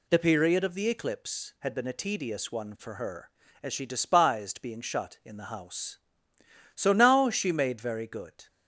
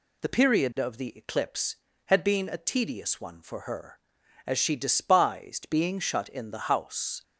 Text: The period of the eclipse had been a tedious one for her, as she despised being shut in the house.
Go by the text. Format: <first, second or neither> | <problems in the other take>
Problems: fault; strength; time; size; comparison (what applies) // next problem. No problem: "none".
second | goes on to say "So now she made very good"; strong; from 6.7 s on; 1.7 s long